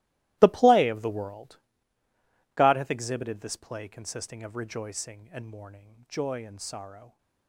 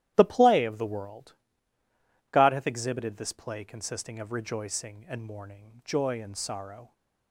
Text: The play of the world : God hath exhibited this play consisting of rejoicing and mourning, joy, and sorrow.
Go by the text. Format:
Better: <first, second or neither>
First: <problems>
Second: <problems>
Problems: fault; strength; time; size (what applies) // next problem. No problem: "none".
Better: second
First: gets quieter; strong; throughout; 16.5 dB // starts louder than the rest; strong; until 1.4 s; 17 dB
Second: starts louder than the rest; strong; until 1.1 s; 12.5 dB